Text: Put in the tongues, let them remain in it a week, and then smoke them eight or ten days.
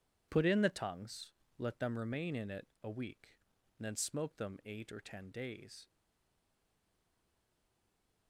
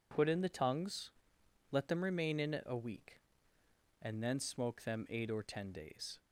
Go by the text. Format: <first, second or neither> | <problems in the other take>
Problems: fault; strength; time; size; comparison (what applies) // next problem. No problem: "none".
second | pauses between "it" and "a"; slight; at 2.6 s; 0.18 s long // stays silent after the last word; from 5.8 s on; 2.4 s long